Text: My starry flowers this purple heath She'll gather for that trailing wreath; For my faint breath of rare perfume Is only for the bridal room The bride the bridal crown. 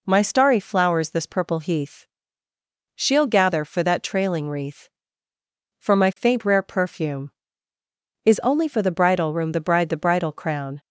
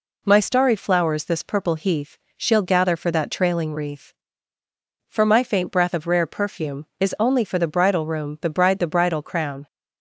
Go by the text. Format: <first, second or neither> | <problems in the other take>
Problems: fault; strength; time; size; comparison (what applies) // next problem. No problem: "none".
second | pauses between "heath" and "She'll"; noticeable; at 2.0 s; 0.90 s long; slight in the second // skips "breath of"; at 6.4 s